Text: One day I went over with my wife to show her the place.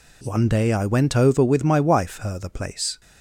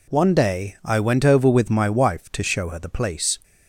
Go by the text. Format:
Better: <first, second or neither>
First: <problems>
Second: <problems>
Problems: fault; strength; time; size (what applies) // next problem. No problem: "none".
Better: second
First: skips "to show"; at 2.1 s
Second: none